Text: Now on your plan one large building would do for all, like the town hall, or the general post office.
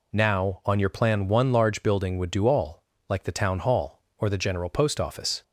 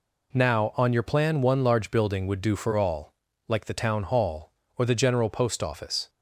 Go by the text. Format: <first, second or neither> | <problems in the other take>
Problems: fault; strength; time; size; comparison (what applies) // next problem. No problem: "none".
second | skips "for"; at 2.4 s